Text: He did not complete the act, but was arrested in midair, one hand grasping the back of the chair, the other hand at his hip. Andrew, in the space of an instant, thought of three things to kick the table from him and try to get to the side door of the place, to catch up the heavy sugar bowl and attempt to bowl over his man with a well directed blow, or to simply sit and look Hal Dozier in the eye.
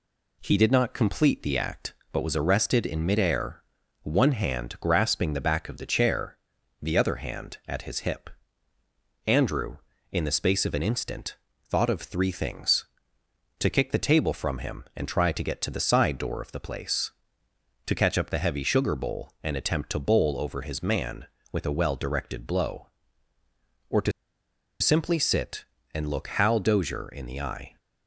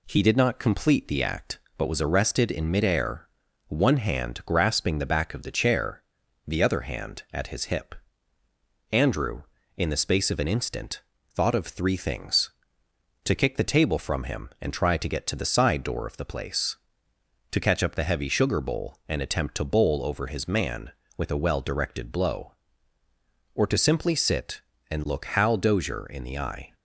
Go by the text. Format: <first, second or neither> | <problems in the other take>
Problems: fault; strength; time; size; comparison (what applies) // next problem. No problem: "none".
second | pauses between "to" and "simply"; noticeable; at 24.1 s; 0.70 s long